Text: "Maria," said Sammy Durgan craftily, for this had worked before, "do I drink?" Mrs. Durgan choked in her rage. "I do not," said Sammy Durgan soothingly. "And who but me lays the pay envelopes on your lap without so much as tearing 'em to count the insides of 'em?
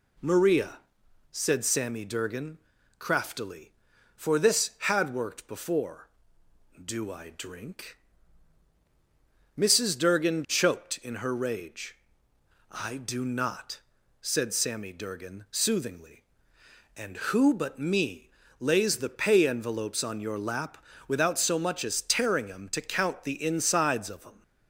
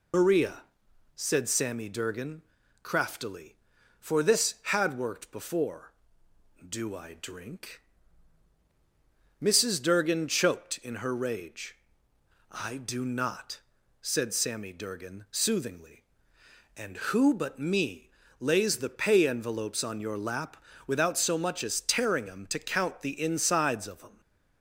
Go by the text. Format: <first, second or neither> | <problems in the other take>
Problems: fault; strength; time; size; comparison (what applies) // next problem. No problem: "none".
first | loses the start of "Maria"; at 0.1 s; 115 ms // pauses between "Durgan" and "craftily"; at 2.4 s; 0.40 s long; also in the first // pauses between "me" and "lays"; slight; at 18.1 s; 0.30 s long; slight in the first // pauses between "lap" and "without"; slight; at 20.6 s; 0.26 s long; slight in the first